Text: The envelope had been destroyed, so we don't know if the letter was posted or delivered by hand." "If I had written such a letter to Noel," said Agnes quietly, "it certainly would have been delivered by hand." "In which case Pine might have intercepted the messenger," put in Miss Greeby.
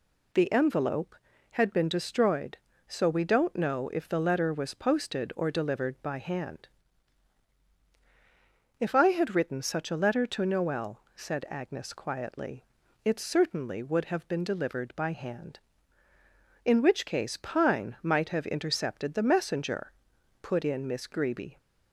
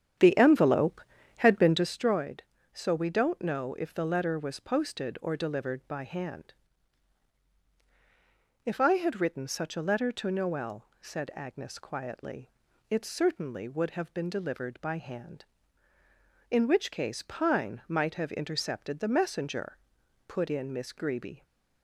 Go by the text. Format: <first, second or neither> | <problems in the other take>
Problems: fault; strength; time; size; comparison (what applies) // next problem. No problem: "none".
first | starts louder than the rest; strong; until 2.0 s; 9 dB